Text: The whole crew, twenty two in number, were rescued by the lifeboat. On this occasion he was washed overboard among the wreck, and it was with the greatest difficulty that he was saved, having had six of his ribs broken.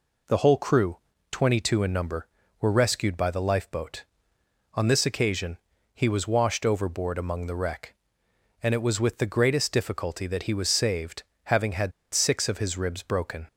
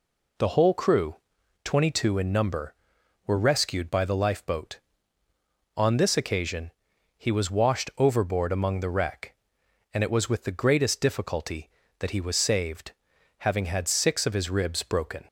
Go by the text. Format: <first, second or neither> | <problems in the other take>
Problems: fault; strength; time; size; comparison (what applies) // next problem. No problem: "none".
second | pauses between "occasion" and "he"; slight; at 5.5 s; 0.36 s long; noticeable in the second // pauses between "had" and "six"; slight; at 11.9 s; 0.21 s long